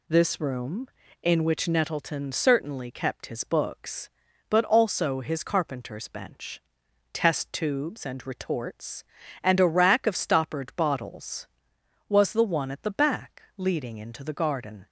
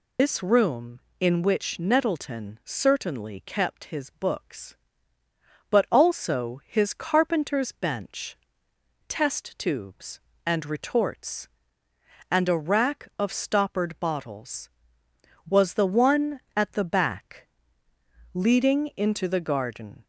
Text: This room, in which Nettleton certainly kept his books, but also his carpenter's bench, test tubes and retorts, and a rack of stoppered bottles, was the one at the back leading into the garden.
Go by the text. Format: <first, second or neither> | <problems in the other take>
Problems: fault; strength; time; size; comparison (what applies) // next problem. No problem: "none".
first | loses the start of "This"; at 0.1 s; 100 ms // pauses between "back" and "leading"; noticeable; at 17.4 s; 0.84 s long; slight in the first